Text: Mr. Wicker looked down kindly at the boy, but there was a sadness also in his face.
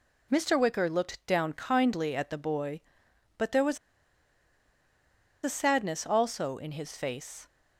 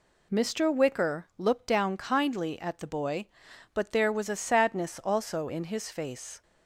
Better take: second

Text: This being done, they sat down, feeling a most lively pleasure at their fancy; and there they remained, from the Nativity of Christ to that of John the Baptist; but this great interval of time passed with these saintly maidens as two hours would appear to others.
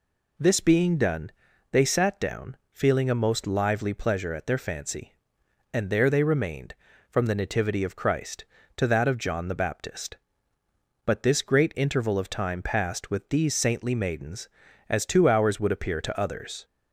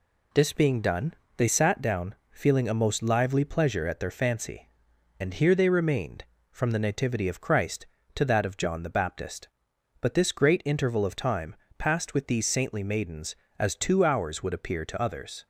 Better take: first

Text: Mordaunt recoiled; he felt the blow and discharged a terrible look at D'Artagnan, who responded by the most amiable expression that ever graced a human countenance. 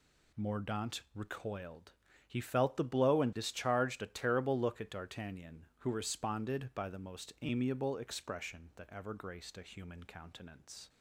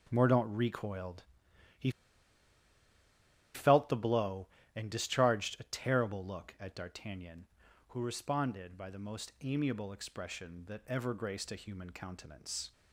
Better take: first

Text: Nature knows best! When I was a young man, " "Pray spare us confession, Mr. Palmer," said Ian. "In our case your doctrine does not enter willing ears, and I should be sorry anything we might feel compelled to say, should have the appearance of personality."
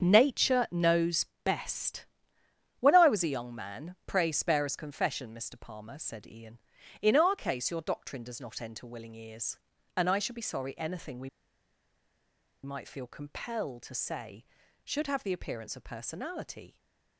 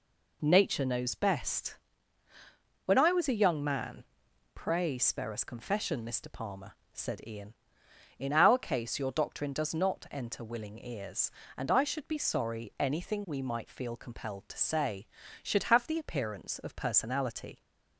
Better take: second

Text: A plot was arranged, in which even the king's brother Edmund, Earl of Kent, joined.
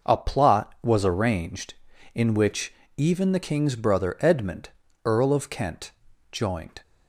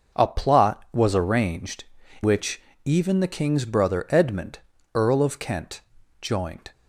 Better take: first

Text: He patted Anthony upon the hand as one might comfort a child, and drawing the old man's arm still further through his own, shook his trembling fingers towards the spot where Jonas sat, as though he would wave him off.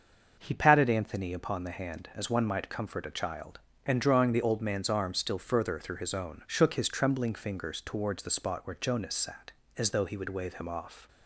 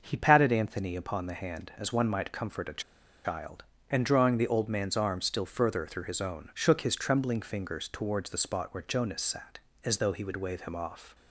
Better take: first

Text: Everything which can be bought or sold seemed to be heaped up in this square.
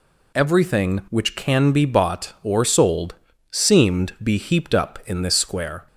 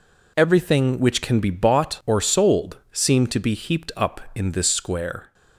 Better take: second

